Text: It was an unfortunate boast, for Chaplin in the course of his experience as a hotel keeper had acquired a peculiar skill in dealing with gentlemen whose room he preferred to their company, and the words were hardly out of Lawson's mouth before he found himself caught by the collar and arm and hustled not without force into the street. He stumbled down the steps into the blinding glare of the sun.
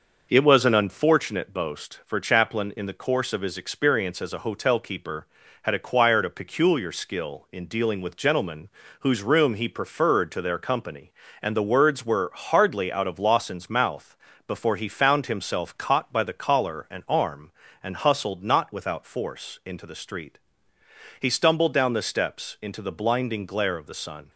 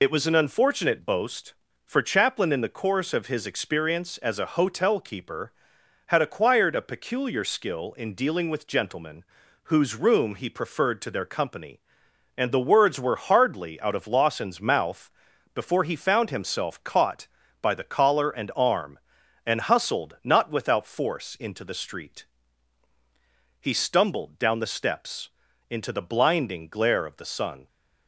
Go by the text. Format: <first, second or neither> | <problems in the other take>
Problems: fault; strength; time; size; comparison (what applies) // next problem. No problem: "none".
first | loses the start of "It"; at 0.0 s; 45 ms // pauses between "gentlemen" and "whose"; at 9.2 s; 0.40 s long; slight in the first // pauses between "mouth" and "before"; noticeable; at 15.0 s; 0.46 s long; slight in the first // pauses between "steps" and "into"; at 25.3 s; 0.40 s long